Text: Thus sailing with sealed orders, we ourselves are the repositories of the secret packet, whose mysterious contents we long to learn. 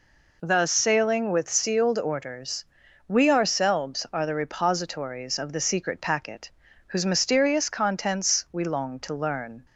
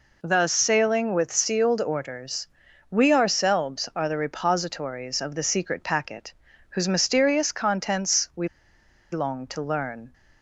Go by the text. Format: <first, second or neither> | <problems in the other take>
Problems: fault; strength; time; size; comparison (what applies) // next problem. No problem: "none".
first | pauses between "we" and "long"; noticeable; at 8.4 s; 0.65 s long